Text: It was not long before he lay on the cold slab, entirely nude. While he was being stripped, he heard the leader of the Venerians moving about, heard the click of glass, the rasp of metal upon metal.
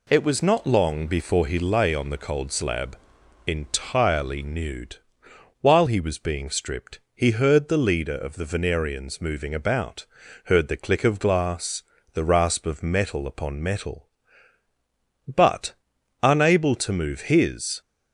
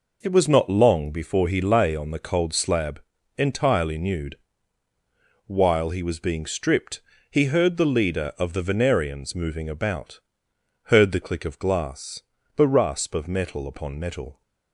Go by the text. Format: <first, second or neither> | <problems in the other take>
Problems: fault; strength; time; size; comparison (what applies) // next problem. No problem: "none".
second | goes on to say "But unable to move his"; strong; from 15.2 s on; 2.5 s long